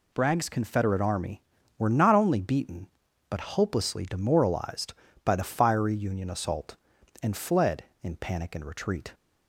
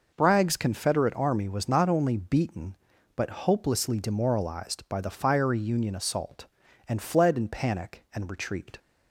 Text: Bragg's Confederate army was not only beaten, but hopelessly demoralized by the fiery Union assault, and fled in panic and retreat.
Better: second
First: says "were" for "was"; at 1.7 s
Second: none

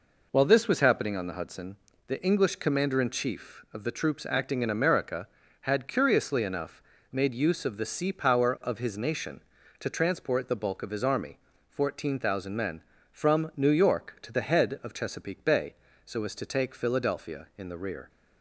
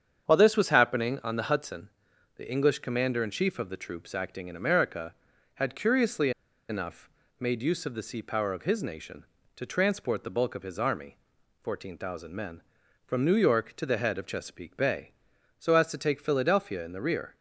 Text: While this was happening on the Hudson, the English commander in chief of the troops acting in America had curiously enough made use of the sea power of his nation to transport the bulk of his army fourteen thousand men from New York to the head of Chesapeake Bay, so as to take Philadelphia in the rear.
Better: first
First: pauses between "enough" and "made"; slight; at 6.8 s; 0.28 s long // pauses between "army" and "fourteen"; slight; at 11.3 s; 0.32 s long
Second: starts louder than the rest; strong; until 1.2 s; 8 dB // pauses between "curiously" and "enough"; at 6.3 s; 0.38 s long // pauses between "enough" and "made"; slight; at 7.0 s; 0.32 s long // pauses between "army" and "fourteen"; at 11.1 s; 0.44 s long

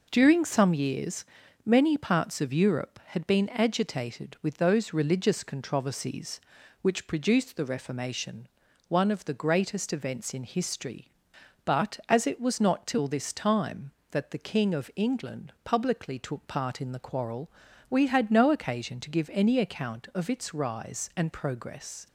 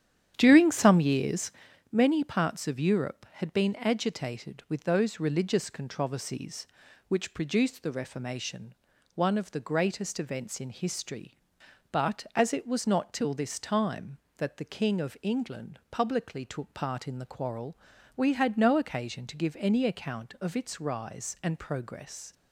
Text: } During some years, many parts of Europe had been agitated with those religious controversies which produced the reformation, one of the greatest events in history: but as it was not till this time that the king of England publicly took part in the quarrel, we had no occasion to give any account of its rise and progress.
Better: first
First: none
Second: starts louder than the rest; strong; until 1.7 s; 10 dB

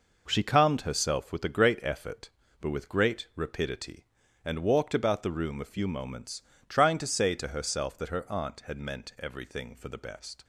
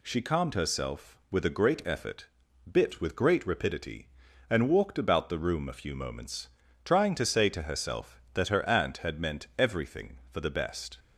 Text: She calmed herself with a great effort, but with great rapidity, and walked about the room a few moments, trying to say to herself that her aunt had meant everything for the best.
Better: first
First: none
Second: says "bit" for "but"; at 2.7 s

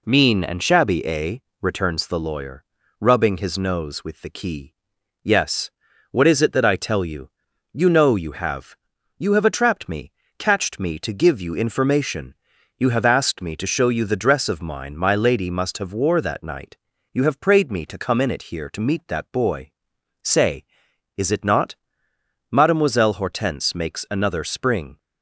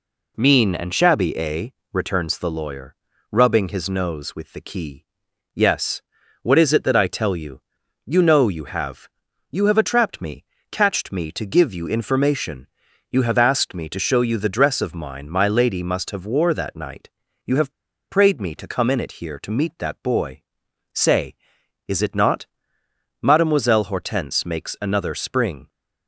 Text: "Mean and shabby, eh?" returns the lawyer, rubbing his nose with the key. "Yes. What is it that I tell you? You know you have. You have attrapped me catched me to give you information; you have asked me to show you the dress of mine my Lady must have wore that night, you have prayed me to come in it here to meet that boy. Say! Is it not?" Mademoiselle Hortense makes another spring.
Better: first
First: pauses between "me" and "catched"; slight; at 10.1 s; 0.28 s long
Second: pauses between "me" and "catched"; slight; at 10.4 s; 0.28 s long // pauses between "have" and "prayed"; at 17.7 s; 0.37 s long

